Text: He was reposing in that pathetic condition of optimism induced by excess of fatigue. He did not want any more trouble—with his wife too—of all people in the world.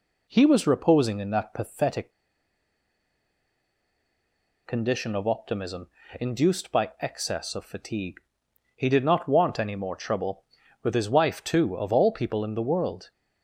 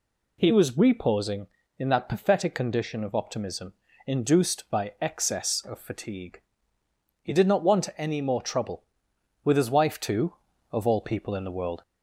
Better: second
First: pauses between "pathetic" and "condition"; strong; at 2.1 s; 2.5 s long // pauses between "optimism" and "induced"; slight; at 5.8 s; 0.30 s long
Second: pauses between "optimism" and "induced"; slight; at 3.7 s; 0.34 s long

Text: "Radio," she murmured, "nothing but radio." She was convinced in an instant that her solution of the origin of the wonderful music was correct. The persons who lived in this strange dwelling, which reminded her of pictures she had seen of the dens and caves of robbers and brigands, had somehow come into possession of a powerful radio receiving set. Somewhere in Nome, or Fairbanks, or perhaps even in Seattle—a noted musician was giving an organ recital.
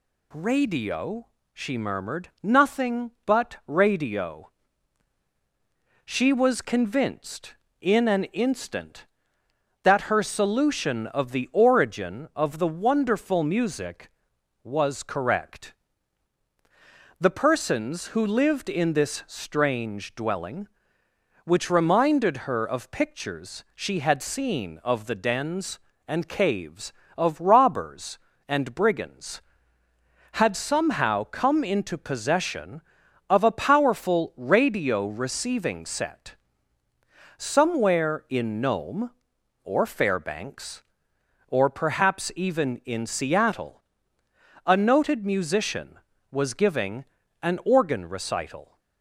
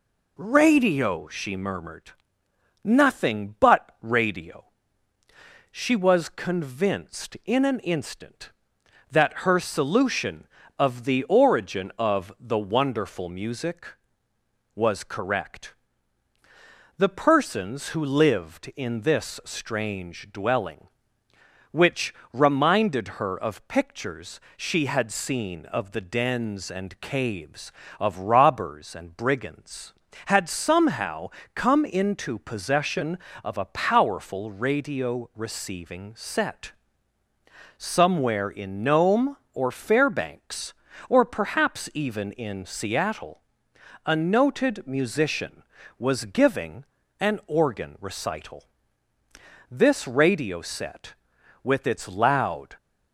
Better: first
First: pauses between "giving" and "an"; at 47.0 s; 0.38 s long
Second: pauses between "which" and "reminded"; slight; at 22.1 s; 0.20 s long // pauses between "pictures" and "she"; slight; at 24.3 s; 0.18 s long // pauses between "somehow" and "come"; slight; at 31.2 s; 0.24 s long // pauses between "giving" and "an"; slight; at 46.8 s; 0.36 s long // goes on to say "This radio set with its loud"; strong; from 49.7 s on; 3.0 s long

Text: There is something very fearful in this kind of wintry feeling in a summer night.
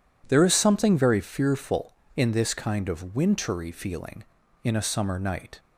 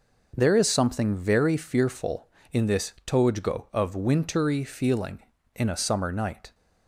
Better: first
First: none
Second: says "tojgo" for "kind"; at 3.0 s

